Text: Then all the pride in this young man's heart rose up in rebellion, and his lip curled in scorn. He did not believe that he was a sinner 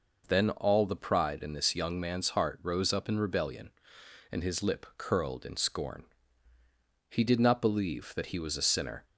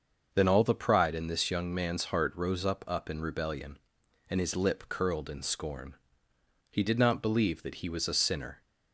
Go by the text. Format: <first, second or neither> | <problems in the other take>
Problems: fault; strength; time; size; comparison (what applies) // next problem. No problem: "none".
first | starts louder than the rest; until 1.3 s; 6.5 dB // says "up" twice; at 2.8 s